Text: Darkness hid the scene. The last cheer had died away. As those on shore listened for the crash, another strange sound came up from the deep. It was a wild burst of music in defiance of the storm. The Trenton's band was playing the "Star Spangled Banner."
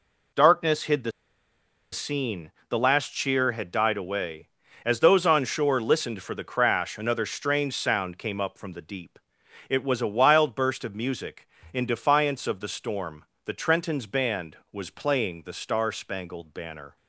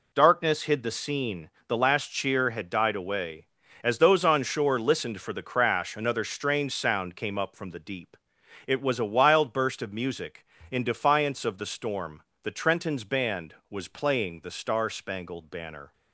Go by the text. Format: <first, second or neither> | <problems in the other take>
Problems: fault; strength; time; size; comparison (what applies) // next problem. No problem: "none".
second | pauses between "the" and "scene"; noticeable; at 1.1 s; 0.81 s long